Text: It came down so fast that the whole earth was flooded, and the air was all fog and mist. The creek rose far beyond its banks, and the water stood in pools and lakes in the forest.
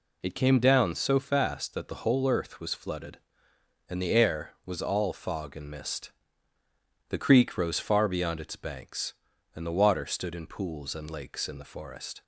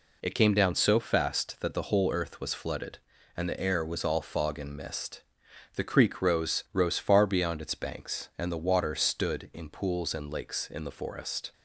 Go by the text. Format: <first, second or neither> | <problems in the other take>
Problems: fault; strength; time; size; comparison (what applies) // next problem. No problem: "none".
first | says "rose" twice; at 6.7 s